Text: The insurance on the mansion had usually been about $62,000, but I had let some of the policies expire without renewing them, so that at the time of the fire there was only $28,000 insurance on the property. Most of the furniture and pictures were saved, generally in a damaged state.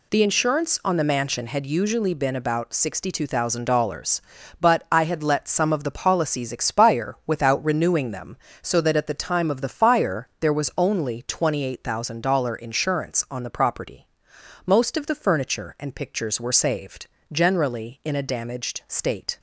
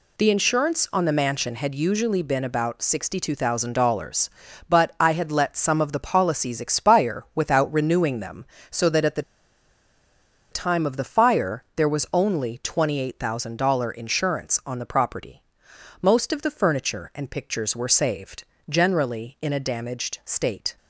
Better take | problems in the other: first | pauses between "the" and "time"; strong; at 9.2 s; 1.3 s long

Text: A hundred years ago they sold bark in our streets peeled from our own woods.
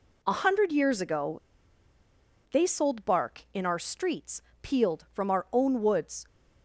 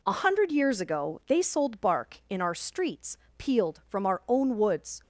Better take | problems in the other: second | pauses between "ago" and "they"; at 1.4 s; 1.1 s long // pauses between "streets" and "peeled"; slight; at 4.4 s; 0.22 s long; slight in the second

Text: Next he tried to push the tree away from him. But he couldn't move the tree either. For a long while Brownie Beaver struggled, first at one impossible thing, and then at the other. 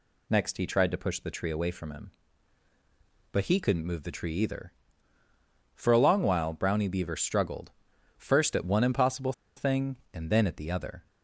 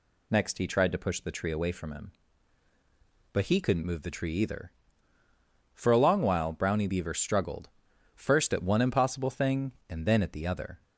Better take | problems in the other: second | pauses between "impossible" and "thing"; slight; at 9.3 s; 0.24 s long

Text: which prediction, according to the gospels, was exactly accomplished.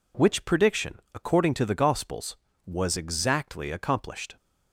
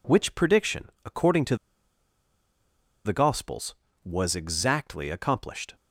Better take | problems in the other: first | pauses between "to" and "the"; strong; at 1.5 s; 1.4 s long

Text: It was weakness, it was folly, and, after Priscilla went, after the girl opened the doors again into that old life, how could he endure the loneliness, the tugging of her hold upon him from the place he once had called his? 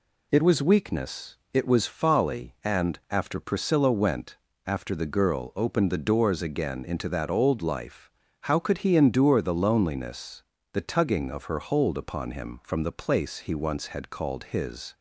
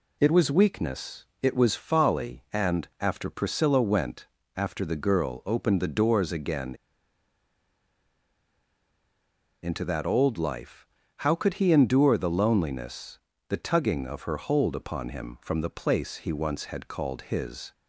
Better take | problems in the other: first | pauses between "again" and "into"; strong; at 6.7 s; 2.8 s long

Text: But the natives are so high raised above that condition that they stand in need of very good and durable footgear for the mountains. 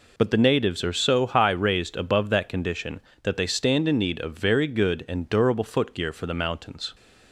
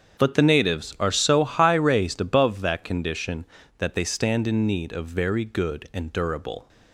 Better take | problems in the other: first | starts louder than the rest; strong; until 1.2 s; 7.5 dB // stops before "footgear for the mountains"; at 6.6 s

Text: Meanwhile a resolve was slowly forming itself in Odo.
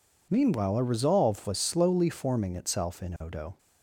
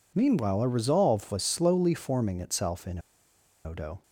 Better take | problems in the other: first | pauses between "in" and "Odo"; noticeable; at 2.9 s; 0.66 s long

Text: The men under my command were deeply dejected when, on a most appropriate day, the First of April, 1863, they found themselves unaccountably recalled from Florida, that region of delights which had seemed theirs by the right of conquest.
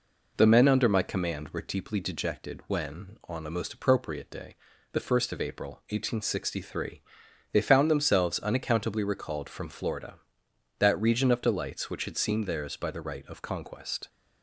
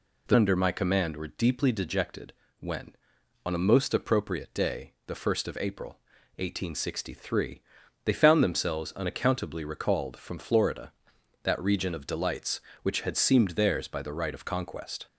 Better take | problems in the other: first | skips "men"; at 0.3 s // pauses between "dejected" and "when"; slight; at 2.3 s; 0.26 s long

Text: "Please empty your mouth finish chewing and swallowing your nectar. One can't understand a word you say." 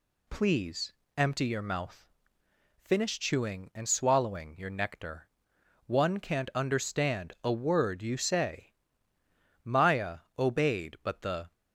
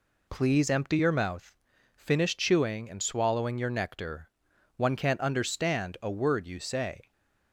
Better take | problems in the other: second | pauses between "Please" and "empty"; slight; at 0.9 s; 0.24 s long // pauses between "mouth" and "finish"; noticeable; at 2.0 s; 0.76 s long; also in the second // goes on to say "Maya obeyed but the"; strong; from 9.6 s on; 1.8 s long

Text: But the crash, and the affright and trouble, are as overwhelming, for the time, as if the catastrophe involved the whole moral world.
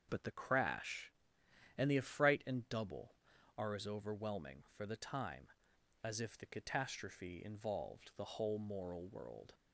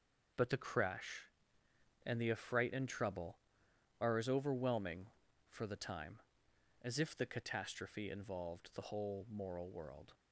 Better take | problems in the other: second | starts louder than the rest; until 1.1 s; 6.5 dB; also in the second // says "double" for "trouble"; at 2.6 s

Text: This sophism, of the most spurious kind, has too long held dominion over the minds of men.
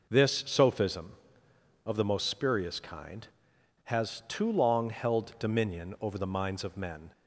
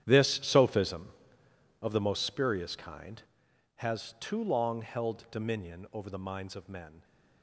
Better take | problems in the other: first | gets quieter; strong; throughout; 16 dB

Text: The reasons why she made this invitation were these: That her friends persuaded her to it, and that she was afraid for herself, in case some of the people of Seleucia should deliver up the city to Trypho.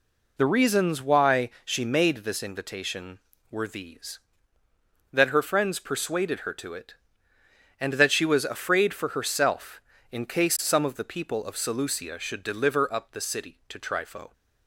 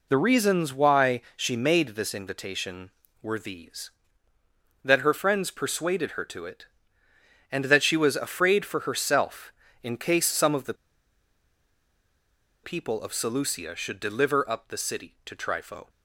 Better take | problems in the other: first | pauses between "the" and "people"; strong; at 10.7 s; 1.8 s long

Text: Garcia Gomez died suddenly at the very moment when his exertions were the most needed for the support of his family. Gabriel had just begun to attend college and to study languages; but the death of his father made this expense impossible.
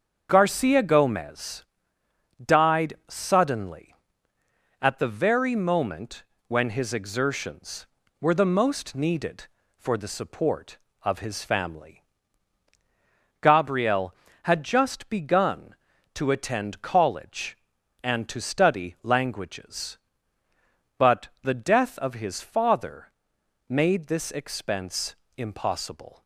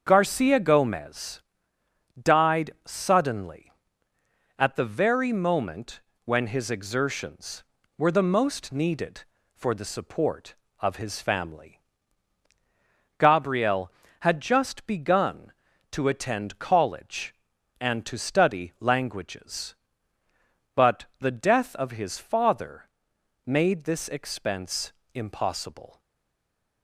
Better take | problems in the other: first | starts louder than the rest; until 1.0 s; 7 dB; also in the first // pauses between "Gomez" and "died"; noticeable; at 1.4 s; 0.76 s long; noticeable in the first // pauses between "died" and "suddenly"; slight; at 2.6 s; 0.16 s long; slight in the first // pauses between "moment" and "when"; slight; at 5.9 s; 0.24 s long; slight in the first // pauses between "but" and "the"; slight; at 21.0 s; 0.16 s long; slight in the first // pauses between "father" and "made"; noticeable; at 22.8 s; 0.58 s long; noticeable in the first // pauses between "expense" and "impossible"; slight; at 24.9 s; 0.20 s long; slight in the first // stays silent after the last word; slight; from 25.9 s on; 0.9 s long

